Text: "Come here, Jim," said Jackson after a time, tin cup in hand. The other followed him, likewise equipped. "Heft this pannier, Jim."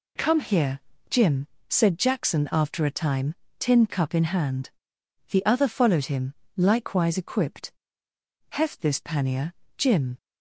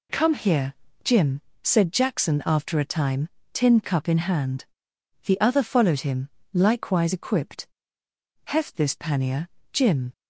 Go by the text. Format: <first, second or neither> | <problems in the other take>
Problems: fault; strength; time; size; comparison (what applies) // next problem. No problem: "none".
neither | none